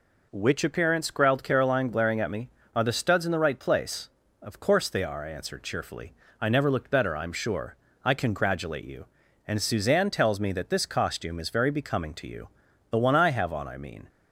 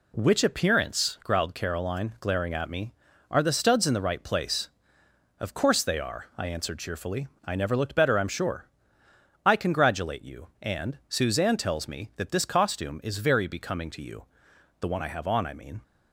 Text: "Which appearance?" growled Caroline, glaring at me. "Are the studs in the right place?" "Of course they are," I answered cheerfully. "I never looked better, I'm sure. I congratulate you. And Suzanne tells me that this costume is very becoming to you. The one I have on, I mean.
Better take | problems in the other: neither | none

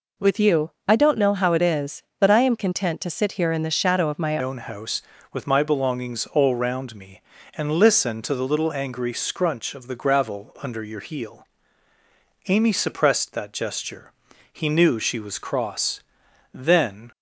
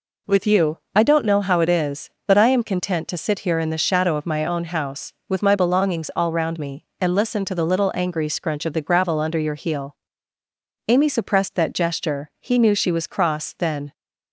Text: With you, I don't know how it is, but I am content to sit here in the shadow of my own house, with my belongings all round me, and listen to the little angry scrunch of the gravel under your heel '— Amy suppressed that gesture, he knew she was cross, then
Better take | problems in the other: second | changes voice at "own"; from 4.4 s on; 12.7 s long

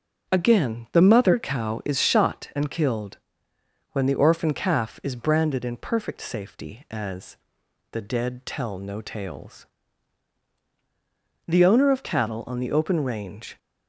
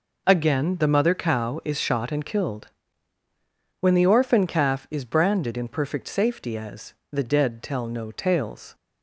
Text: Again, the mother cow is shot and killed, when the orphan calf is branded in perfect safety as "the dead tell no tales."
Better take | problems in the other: second | starts louder than the rest; until 1.3 s; 6.5 dB // pauses between "as" and "the"; noticeable; at 7.3 s; 0.54 s long; slight in the second // goes on to say "The owner of cattle on the open range"; strong; from 11.4 s on; 2.1 s long

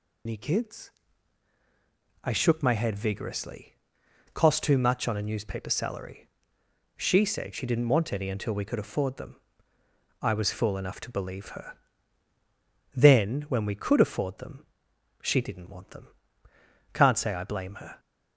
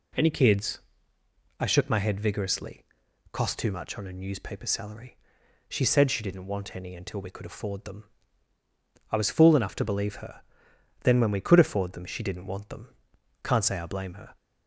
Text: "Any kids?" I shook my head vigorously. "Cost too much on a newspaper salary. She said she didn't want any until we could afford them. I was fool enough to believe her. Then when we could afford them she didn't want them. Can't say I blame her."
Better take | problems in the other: second | loses the start of "Any"; at 0.2 s; 100 ms // pauses between "them" and "she"; noticeable; at 14.6 s; 0.56 s long

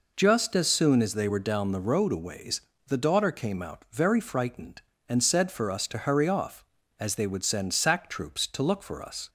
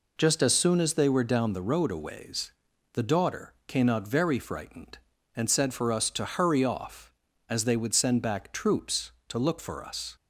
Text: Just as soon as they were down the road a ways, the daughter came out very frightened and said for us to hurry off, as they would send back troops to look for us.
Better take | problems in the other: second | says "sack" for "back"; at 7.7 s

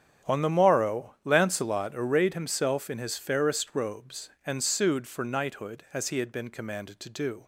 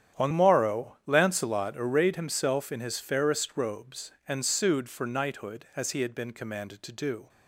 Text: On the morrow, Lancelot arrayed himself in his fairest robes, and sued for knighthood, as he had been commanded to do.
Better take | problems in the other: first | starts louder than the rest; strong; until 1.2 s; 9.5 dB; strong in the first // skips "the"; at 0.3 s

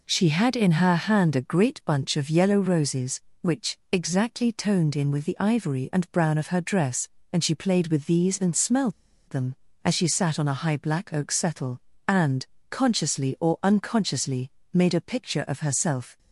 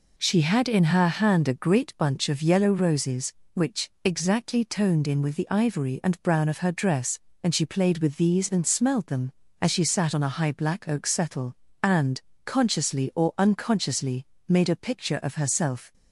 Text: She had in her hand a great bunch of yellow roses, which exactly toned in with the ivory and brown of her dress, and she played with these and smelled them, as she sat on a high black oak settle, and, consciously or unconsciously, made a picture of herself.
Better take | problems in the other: second | pauses between "smelled" and "them"; at 8.9 s; 0.36 s long

